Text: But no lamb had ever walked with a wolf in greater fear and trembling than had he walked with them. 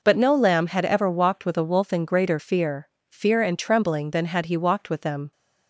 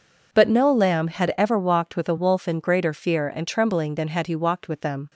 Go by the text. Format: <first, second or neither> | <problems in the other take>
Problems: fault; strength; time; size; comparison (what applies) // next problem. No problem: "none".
second | says "fear" twice; at 3.0 s